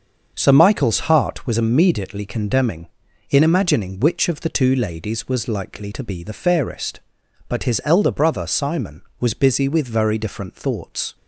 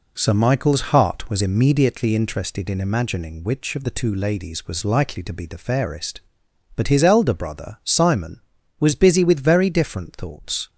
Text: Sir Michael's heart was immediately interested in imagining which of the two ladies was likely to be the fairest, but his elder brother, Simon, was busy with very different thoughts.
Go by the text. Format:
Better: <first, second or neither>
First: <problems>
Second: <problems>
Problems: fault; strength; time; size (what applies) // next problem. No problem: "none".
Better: second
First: starts louder than the rest; until 1.3 s; 6.5 dB // says "condemning" for "interested"; at 2.2 s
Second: none